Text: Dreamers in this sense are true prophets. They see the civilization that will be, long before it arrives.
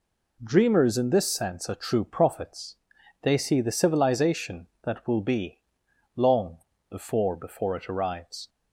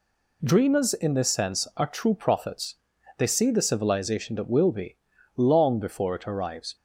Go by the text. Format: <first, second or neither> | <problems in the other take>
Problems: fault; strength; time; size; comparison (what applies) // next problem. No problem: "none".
second | pauses between "long" and "before"; slight; at 6.5 s; 0.30 s long // says "before" twice; at 7.3 s